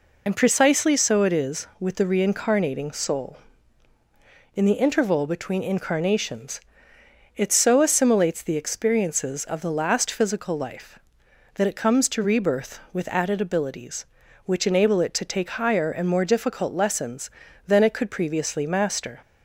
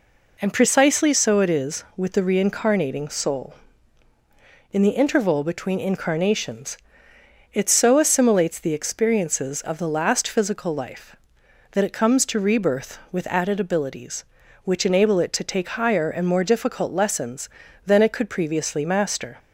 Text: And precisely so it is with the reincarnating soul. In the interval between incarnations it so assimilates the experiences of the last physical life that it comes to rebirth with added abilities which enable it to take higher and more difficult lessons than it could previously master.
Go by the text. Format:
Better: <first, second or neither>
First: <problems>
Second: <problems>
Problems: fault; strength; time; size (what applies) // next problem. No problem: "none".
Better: second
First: loses the start of "And"; at 0.2 s; 35 ms // pauses between "incarnations" and "it"; noticeable; at 6.6 s; 0.76 s long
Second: pauses between "incarnations" and "it"; noticeable; at 6.7 s; 0.76 s long